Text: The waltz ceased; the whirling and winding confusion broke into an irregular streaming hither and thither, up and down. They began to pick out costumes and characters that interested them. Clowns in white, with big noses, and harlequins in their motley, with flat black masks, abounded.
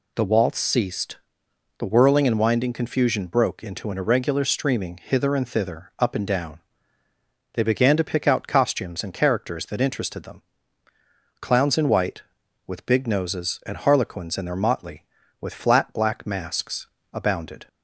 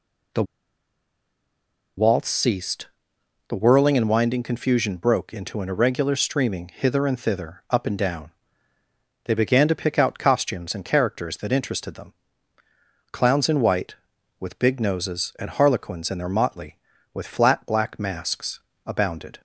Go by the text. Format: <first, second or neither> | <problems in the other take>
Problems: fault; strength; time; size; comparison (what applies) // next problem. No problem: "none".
first | pauses between "The" and "waltz"; strong; at 0.4 s; 1.5 s long